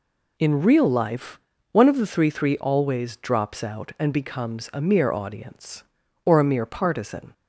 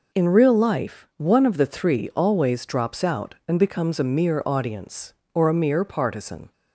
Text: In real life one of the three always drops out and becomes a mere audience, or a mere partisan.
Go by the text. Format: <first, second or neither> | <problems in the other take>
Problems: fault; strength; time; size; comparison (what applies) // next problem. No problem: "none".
second | pauses between "life" and "one"; slight; at 1.3 s; 0.32 s long // says "three" twice; at 2.2 s